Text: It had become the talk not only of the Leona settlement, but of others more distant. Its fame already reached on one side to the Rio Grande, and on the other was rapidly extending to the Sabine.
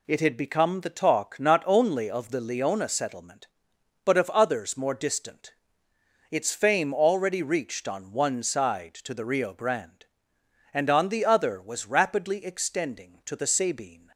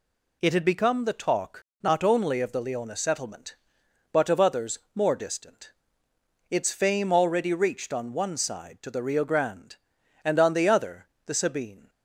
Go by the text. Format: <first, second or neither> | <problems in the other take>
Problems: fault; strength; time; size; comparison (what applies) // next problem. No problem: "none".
first | pauses between "talk" and "not"; slight; at 1.6 s; 0.18 s long // pauses between "others" and "more"; slight; at 4.7 s; 0.16 s long // skips "was rapidly extending to"; at 11.1 s